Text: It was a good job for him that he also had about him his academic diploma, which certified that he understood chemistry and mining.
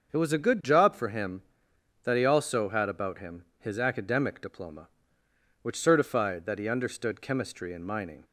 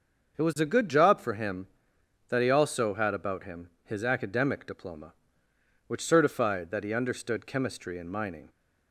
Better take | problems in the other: neither | starts louder than the rest; the same in both // pauses between "him" and "his"; slight; the same in both

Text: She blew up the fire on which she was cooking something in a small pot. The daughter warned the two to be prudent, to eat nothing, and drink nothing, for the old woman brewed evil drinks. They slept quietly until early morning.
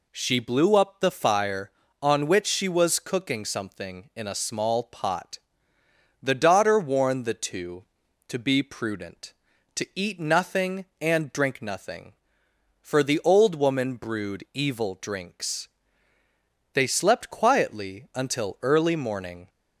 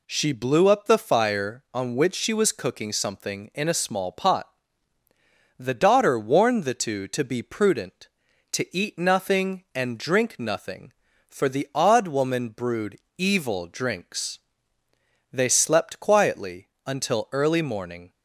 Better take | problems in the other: first | says "odd" for "old"; at 11.7 s // pauses between "brewed" and "evil"; slight; at 12.9 s; 0.20 s long // pauses between "quietly" and "until"; slight; at 16.6 s; 0.18 s long

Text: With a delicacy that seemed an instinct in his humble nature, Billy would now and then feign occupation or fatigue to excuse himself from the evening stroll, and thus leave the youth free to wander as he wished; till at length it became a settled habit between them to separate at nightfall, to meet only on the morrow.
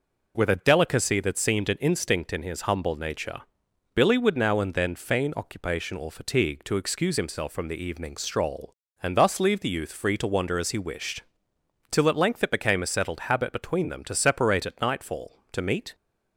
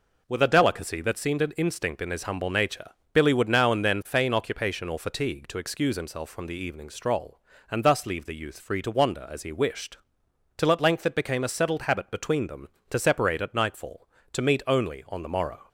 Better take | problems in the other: second | stops before "only on the morrow"; at 15.9 s

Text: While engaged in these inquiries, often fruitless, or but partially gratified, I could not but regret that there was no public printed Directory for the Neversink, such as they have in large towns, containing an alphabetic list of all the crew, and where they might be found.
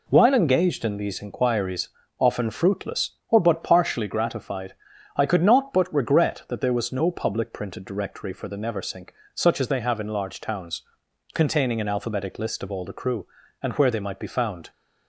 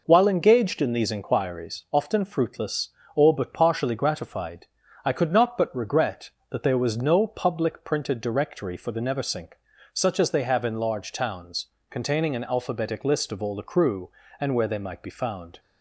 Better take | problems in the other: neither | none

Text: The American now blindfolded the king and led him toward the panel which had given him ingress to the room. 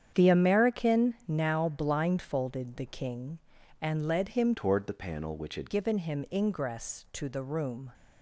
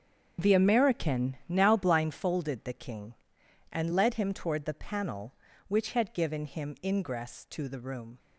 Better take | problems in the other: second | starts louder than the rest; strong; until 1.2 s; 8.5 dB; strong in the second // changes voice from "toward" to "had"; from 4.5 to 5.7 s; 1.2 s long

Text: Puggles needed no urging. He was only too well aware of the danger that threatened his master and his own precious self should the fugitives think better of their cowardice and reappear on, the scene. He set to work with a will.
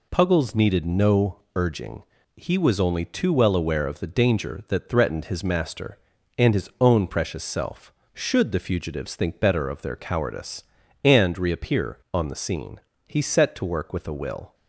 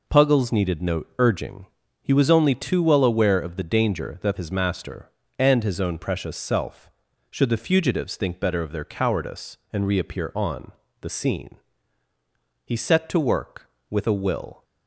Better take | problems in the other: first | skips "threatened"; at 4.3 s

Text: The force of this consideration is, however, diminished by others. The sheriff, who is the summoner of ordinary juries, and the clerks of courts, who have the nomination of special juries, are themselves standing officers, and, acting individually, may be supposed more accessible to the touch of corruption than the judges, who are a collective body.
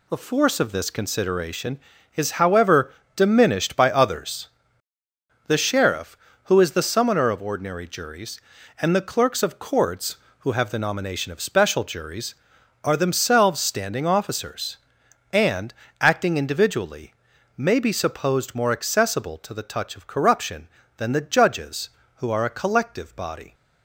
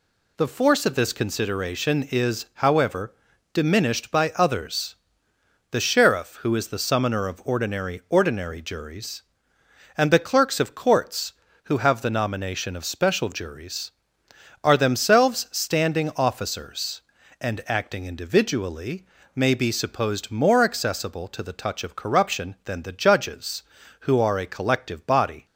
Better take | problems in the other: first | says "ordinary" twice; at 8.0 s

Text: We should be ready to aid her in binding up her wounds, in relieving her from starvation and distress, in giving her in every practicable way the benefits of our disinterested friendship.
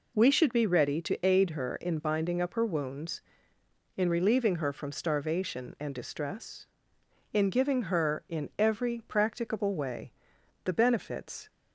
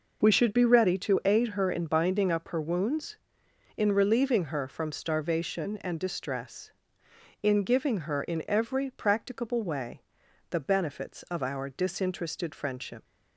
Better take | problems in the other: second | pauses between "way" and "the"; noticeable; at 10.1 s; 0.54 s long; noticeable in the second // stops before "of our disinterested friendship"; at 11.4 s

